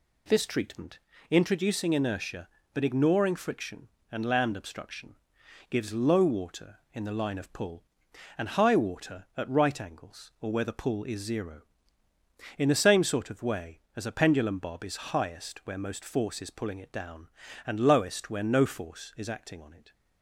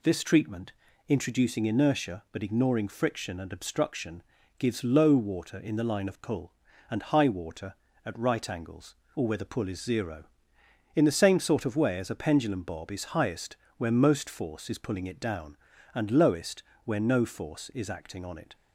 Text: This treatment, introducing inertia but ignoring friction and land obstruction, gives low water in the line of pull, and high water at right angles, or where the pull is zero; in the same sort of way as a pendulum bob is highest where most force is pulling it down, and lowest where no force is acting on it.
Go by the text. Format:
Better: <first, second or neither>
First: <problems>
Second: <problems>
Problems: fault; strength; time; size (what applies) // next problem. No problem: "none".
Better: first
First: none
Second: skips "land"; at 3.5 s // pauses between "highest" and "where"; slight; at 13.5 s; 0.20 s long // pauses between "lowest" and "where"; slight; at 16.6 s; 0.22 s long